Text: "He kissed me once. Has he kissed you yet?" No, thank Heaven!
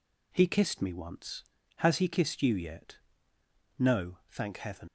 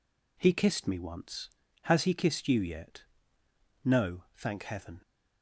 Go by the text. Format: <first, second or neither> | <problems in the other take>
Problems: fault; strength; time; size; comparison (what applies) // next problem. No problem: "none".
second | leaves "Heaven" unfinished; at 4.8 s; 75 ms